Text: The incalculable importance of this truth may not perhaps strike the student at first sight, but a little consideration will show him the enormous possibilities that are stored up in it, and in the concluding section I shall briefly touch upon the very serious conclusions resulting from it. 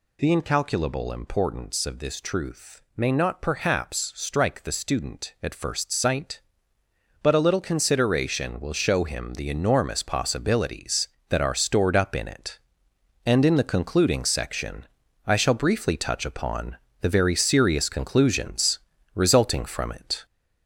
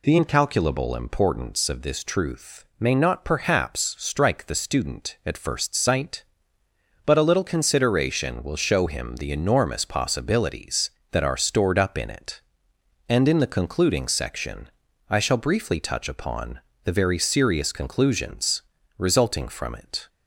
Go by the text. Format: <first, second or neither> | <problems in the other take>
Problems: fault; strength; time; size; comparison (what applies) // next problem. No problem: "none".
second | gets louder; noticeable; throughout; 4 dB // pauses between "section" and "I"; at 14.8 s; 0.38 s long; also in the second // pauses between "upon" and "the"; slight; at 16.7 s; 0.24 s long; slight in the second // pauses between "conclusions" and "resulting"; slight; at 18.7 s; 0.36 s long; slight in the second